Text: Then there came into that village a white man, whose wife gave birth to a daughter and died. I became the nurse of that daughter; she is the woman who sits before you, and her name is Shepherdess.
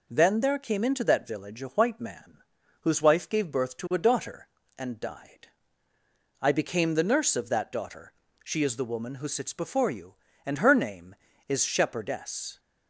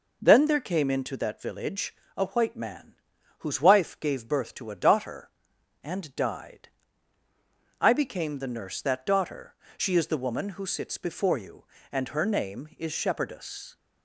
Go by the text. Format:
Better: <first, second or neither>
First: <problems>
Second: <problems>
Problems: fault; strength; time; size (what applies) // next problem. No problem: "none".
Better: first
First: none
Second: pauses between "village" and "a"; slight; at 1.9 s; 0.24 s long // skips "of"; at 8.8 s